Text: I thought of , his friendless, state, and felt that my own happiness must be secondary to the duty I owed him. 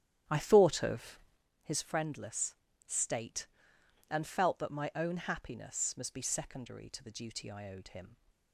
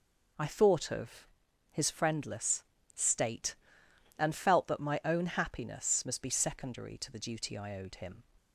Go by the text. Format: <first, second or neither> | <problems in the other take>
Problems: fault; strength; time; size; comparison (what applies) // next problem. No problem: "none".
second | starts louder than the rest; strong; until 1.5 s; 10.5 dB